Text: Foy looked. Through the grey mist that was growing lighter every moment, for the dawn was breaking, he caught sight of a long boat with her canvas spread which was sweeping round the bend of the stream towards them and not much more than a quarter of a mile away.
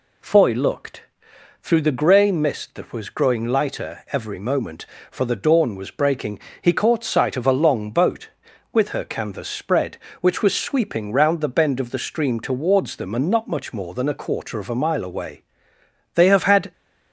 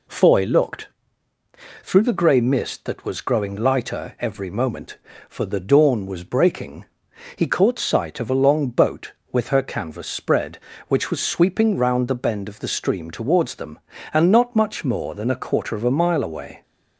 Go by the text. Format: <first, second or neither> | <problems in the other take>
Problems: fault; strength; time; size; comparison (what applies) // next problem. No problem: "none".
second | goes on to say "They have had"; from 16.1 s on; 0.58 s long